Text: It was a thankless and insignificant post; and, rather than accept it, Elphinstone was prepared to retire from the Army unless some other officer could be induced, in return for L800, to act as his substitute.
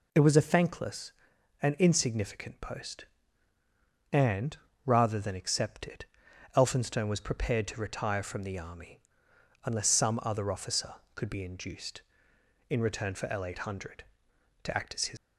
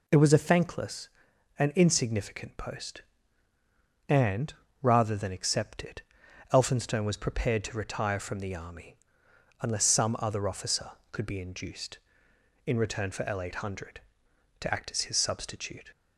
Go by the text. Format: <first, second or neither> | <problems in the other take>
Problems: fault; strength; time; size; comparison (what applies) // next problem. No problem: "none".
second | pauses between "Army" and "unless"; noticeable; at 8.9 s; 0.66 s long; noticeable in the second // stops before "substitute"; at 15.1 s